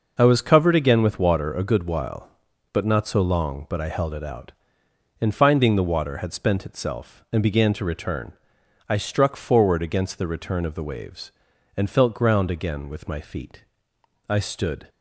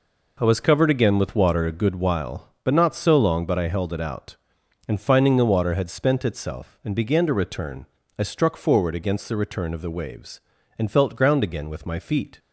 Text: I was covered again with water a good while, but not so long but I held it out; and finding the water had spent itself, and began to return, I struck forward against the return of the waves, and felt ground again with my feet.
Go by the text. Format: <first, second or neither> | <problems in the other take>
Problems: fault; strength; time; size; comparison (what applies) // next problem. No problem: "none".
second | goes on to say "I stood"; from 14.2 s on; 0.60 s long